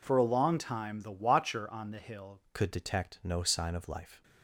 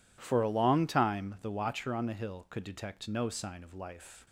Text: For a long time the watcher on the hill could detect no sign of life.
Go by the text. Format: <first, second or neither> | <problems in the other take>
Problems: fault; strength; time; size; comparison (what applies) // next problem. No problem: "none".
second | changes voice at "could"; from 2.5 s on; 1.7 s long